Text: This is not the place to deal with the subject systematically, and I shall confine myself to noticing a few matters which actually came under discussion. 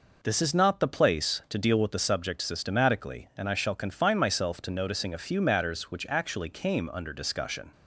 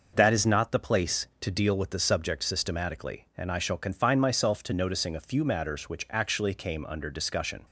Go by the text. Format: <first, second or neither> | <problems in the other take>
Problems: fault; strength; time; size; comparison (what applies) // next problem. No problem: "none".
first | says "That" for "This"; at 0.1 s